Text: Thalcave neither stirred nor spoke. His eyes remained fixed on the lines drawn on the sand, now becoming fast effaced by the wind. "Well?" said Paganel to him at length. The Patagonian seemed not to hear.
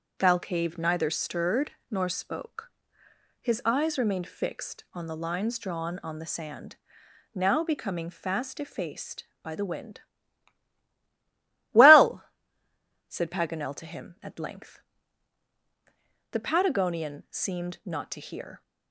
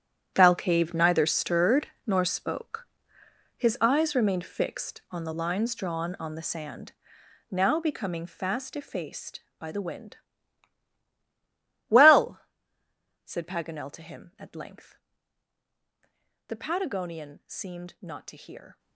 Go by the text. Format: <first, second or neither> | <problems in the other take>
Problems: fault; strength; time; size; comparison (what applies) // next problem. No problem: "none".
first | gets quieter; strong; throughout; 13.5 dB // starts louder than the rest; strong; until 1.3 s; 10 dB; also in the first // pauses between "stirred" and "nor"; slight; at 1.8 s; 0.18 s long; slight in the first